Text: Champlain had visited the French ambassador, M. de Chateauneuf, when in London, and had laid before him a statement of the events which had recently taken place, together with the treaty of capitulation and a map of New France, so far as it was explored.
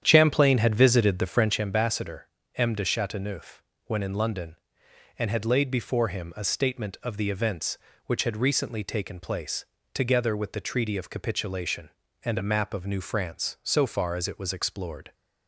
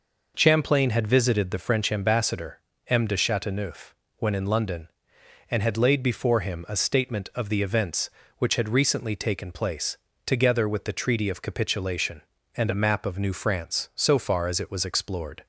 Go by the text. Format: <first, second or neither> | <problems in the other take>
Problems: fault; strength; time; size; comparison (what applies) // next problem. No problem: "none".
second | starts louder than the rest; strong; until 1.7 s; 9.5 dB